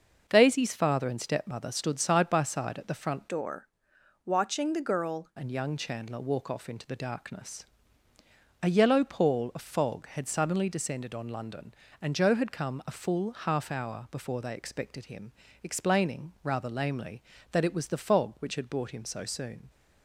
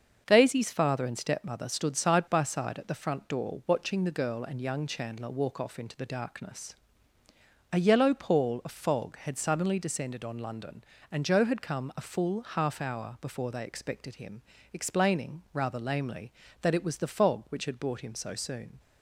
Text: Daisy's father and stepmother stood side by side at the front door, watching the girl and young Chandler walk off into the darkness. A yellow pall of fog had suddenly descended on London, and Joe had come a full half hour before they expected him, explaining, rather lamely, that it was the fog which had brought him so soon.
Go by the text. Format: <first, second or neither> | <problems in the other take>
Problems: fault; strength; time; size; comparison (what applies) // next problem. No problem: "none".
second | starts louder than the rest; noticeable; until 1.2 s; 6 dB; also in the second // changes voice from "door" to "girl"; from 3.2 to 5.2 s; 2.0 s long